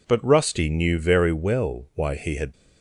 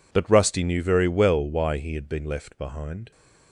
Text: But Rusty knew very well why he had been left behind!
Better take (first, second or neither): second